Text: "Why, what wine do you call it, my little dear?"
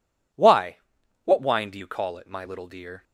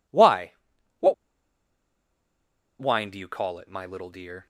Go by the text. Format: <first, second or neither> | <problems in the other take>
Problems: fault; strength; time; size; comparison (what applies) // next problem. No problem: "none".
first | pauses between "what" and "wine"; strong; at 1.1 s; 1.6 s long